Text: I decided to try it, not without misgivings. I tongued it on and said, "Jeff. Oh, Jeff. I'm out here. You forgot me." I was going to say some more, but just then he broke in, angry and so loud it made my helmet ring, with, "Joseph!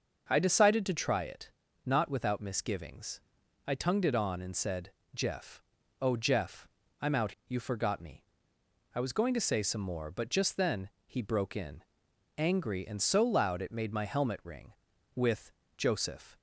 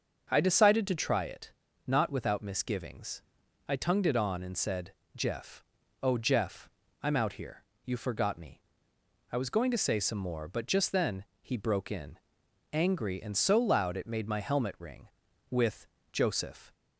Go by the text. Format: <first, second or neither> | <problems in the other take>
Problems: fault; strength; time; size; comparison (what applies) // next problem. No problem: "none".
second | starts louder than the rest; until 1.3 s; 6.5 dB; also in the second // skips "here"; at 7.4 s // pauses between "then" and "he"; slight; at 10.8 s; 0.16 s long; slight in the second